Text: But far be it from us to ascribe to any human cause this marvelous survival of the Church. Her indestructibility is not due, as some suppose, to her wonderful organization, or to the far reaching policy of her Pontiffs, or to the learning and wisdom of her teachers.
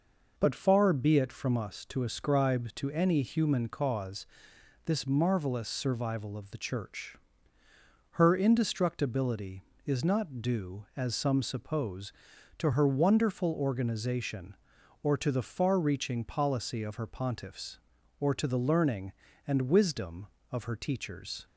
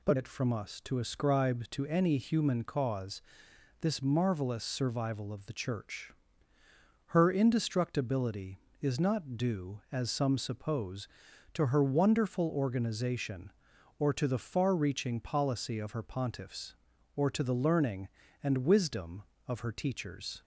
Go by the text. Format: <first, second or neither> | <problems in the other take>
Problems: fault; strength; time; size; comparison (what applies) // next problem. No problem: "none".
first | skips "far be"; at 0.1 s // pauses between "cause" and "this"; noticeable; at 3.2 s; 0.58 s long; noticeable in the first